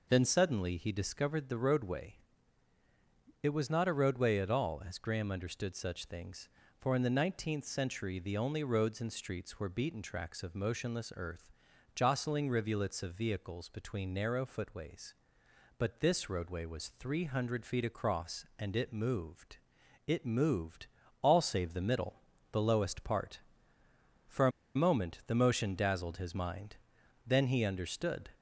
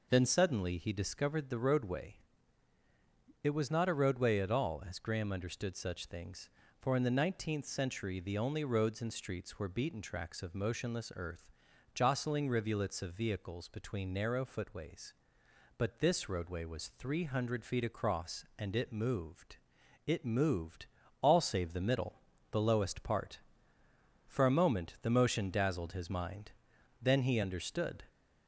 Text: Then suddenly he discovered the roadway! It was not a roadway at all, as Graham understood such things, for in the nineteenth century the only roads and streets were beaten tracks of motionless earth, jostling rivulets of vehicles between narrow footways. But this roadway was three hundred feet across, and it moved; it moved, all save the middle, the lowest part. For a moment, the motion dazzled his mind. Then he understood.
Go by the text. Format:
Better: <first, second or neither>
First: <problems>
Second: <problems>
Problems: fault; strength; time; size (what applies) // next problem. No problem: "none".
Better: second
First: pauses between "a" and "moment"; slight; at 24.5 s; 0.24 s long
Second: none